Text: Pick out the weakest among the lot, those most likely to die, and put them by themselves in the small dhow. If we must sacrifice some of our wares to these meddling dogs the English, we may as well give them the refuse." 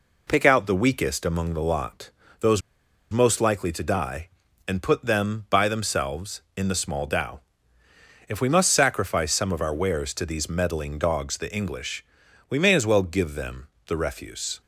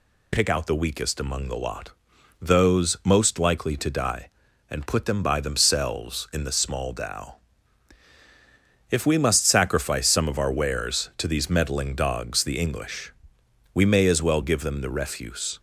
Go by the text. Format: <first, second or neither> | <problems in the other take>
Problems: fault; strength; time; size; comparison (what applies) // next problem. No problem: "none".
second | pauses between "those" and "most"; noticeable; at 2.6 s; 0.51 s long // pauses between "them" and "the"; slight; at 13.6 s; 0.20 s long